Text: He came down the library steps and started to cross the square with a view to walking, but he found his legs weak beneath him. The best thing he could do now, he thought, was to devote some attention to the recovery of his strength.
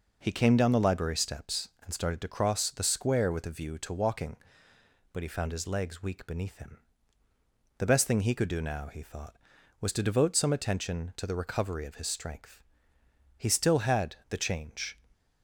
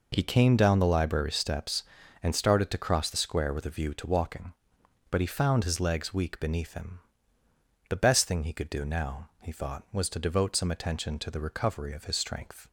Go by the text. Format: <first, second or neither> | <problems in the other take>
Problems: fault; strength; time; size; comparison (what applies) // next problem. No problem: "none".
second | goes on to say "He still had the change"; from 13.3 s on; 1.6 s long